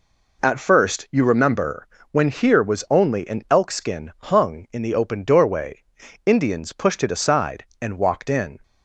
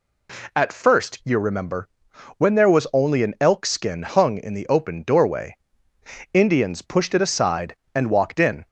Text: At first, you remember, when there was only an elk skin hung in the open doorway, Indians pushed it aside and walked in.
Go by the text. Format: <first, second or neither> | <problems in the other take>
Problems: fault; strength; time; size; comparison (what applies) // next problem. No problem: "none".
second | says "here" for "there"; at 2.3 s